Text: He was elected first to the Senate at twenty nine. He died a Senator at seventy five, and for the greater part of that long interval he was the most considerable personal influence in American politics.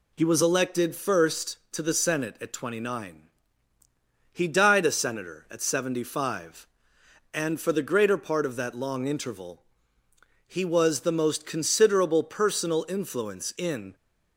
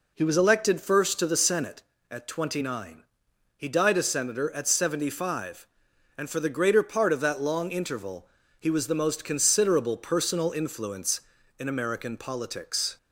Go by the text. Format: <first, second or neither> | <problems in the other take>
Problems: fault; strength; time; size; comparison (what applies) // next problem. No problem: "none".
second | pauses between "interval" and "he"; noticeable; at 9.6 s; 0.86 s long; slight in the second // stops before "American politics"; at 13.9 s